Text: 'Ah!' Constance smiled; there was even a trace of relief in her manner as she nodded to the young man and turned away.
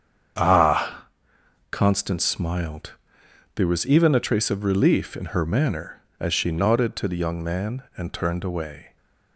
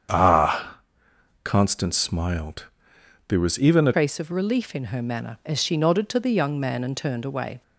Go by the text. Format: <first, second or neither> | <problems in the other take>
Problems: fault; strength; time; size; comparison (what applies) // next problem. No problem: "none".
first | starts louder than the rest; strong; until 1.7 s; 8 dB; strong in the first // changes voice at "trace"; from 3.9 s on; 3.7 s long